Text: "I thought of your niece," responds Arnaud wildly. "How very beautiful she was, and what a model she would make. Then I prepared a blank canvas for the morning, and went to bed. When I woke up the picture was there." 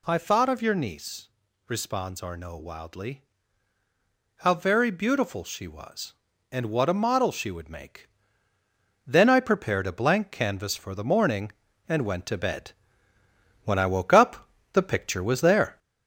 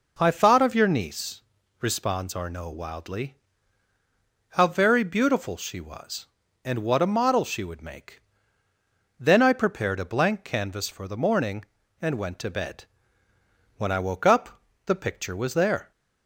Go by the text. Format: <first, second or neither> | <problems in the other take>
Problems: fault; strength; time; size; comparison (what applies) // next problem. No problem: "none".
second | gets louder; slight; throughout; 3 dB // pauses between "up" and "the"; slight; at 14.4 s; 0.26 s long; slight in the second